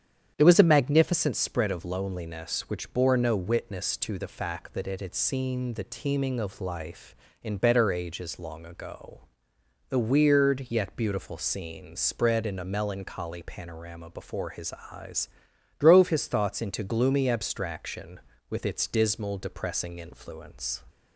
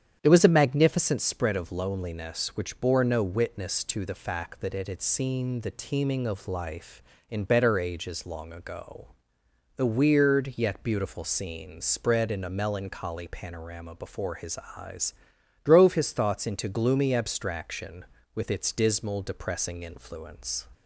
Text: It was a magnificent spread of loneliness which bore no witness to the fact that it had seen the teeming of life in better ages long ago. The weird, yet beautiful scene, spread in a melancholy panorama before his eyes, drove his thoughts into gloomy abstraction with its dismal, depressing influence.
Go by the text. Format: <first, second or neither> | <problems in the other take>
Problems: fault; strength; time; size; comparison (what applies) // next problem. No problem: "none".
neither | starts louder than the rest; strong; the same in both // pauses between "his" and "eyes"; slight; the same in both